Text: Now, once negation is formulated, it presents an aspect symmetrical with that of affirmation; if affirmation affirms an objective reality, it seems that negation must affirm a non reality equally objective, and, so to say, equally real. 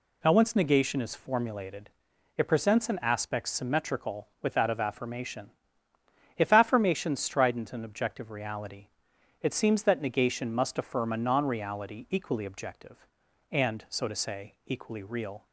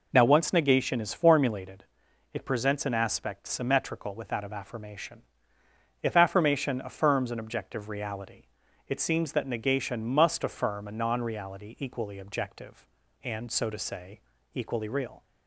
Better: second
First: says "strident" for "affirms"; at 7.1 s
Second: none

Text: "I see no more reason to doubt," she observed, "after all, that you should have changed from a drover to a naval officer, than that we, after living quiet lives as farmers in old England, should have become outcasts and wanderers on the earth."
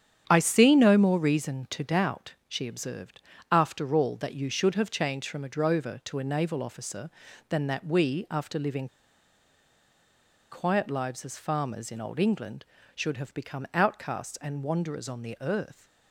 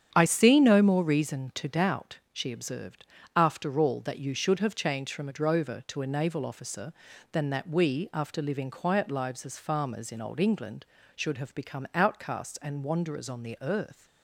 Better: second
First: starts louder than the rest; strong; until 1.3 s; 8.5 dB // pauses between "living" and "quiet"; strong; at 8.8 s; 1.6 s long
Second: starts louder than the rest; strong; until 1.1 s; 8.5 dB

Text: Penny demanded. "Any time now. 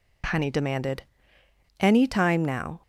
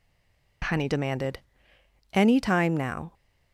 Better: first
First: none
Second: stays silent before the first word; slight; until 0.6 s; 0.6 s long

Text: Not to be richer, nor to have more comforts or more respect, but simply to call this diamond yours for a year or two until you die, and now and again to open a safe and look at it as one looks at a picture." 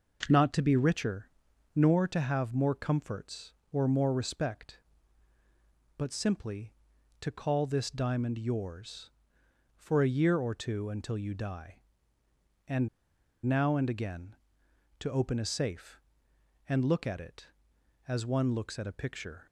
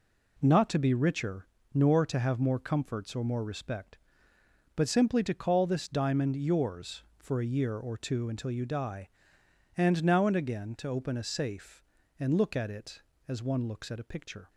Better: second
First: pauses between "and" and "now"; noticeable; at 12.8 s; 0.57 s long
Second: none

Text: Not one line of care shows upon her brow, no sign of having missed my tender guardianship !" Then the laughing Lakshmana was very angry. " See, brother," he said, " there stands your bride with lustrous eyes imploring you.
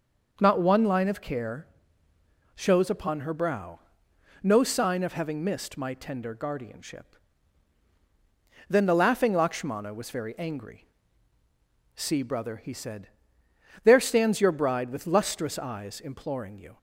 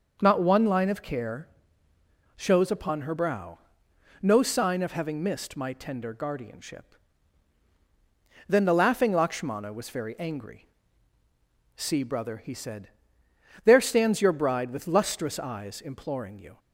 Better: neither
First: starts louder than the rest; until 1.4 s; 6.5 dB // pauses between "care" and "shows"; noticeable; at 1.6 s; 0.90 s long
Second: starts louder than the rest; until 1.2 s; 6.5 dB // pauses between "care" and "shows"; noticeable; at 1.4 s; 0.90 s long

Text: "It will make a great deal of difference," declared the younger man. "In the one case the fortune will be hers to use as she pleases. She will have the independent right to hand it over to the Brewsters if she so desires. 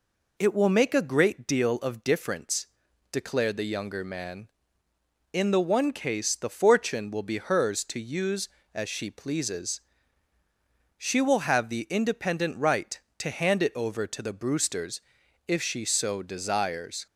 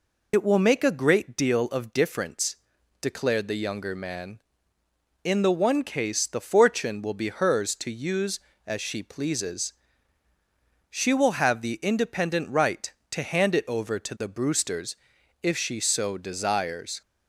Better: first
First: pauses between "Brewsters" and "if"; noticeable; at 15.0 s; 0.46 s long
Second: loses the start of "It"; at 0.3 s; 50 ms // pauses between "Brewsters" and "if"; noticeable; at 14.9 s; 0.46 s long

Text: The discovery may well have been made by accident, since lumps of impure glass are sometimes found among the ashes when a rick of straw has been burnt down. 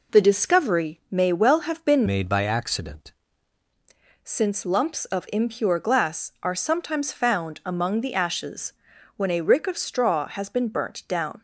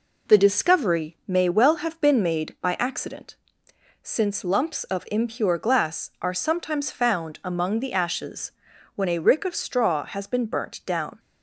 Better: second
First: changes voice from "made" to "accident"; from 2.0 to 3.1 s; 1.1 s long // pauses between "ashes" and "when"; noticeable; at 8.7 s; 0.46 s long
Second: pauses between "ashes" and "when"; noticeable; at 8.4 s; 0.46 s long

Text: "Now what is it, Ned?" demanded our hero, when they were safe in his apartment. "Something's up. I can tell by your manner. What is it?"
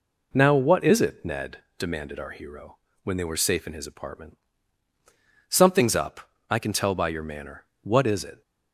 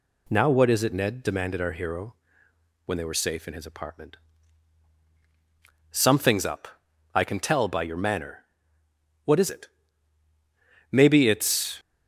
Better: first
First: none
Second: goes on to say "Maybe it's"; noticeable; from 10.9 s on; 0.88 s long

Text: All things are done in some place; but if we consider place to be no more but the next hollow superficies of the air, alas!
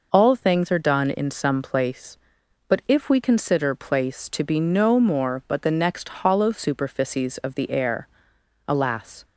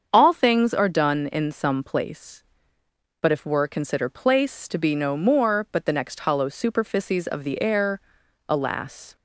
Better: first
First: none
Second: starts louder than the rest; strong; until 1.1 s; 7 dB // says "were" for "we"; at 3.4 s

